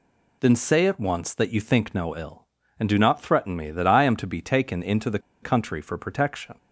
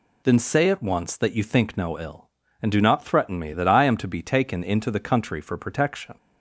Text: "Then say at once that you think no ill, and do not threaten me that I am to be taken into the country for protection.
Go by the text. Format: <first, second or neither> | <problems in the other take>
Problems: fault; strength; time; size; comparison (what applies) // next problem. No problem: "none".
second | pauses between "the" and "country"; slight; at 5.1 s; 0.22 s long